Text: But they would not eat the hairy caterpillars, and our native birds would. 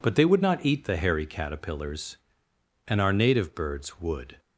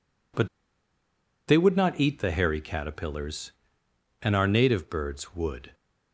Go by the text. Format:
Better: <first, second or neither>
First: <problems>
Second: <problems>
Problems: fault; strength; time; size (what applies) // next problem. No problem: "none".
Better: first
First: none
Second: pauses between "But" and "they"; at 0.4 s; 0.99 s long